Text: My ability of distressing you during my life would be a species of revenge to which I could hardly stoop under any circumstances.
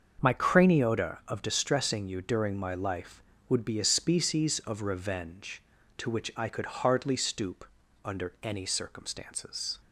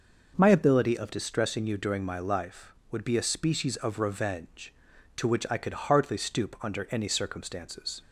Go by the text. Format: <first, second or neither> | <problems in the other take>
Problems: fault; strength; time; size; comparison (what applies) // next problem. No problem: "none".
second | starts louder than the rest; until 1.3 s; 7 dB // says "craniota" for "ability"; at 0.3 s // pauses between "stoop" and "under"; at 7.6 s; 0.40 s long